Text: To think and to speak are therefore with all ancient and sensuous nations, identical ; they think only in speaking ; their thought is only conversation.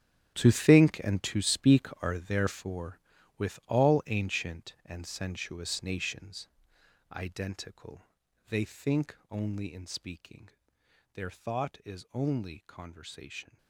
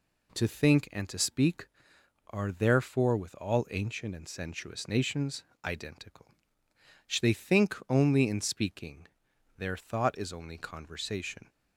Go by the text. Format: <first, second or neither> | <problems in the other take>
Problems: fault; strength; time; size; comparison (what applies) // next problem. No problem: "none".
second | gets quieter; strong; throughout; 15 dB